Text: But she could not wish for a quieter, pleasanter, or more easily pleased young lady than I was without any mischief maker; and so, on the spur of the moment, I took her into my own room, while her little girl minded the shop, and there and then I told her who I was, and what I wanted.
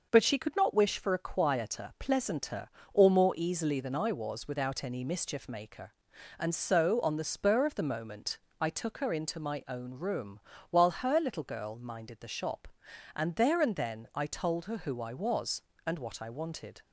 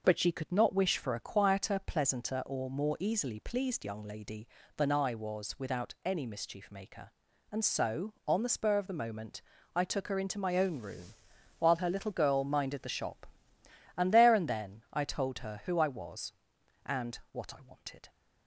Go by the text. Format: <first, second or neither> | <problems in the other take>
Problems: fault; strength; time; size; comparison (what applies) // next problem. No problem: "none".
second | skips "pleased young lady"; at 3.8 s